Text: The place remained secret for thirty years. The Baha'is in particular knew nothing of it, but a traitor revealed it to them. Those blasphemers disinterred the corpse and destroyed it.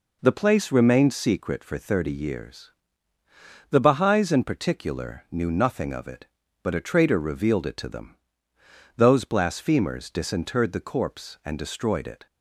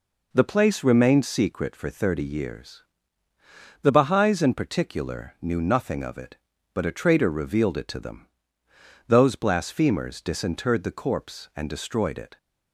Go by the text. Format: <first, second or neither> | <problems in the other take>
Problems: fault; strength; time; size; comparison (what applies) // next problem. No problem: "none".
neither | none